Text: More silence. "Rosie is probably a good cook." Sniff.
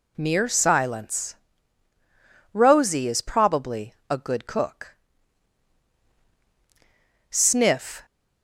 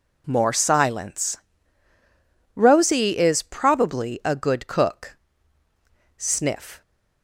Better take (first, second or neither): second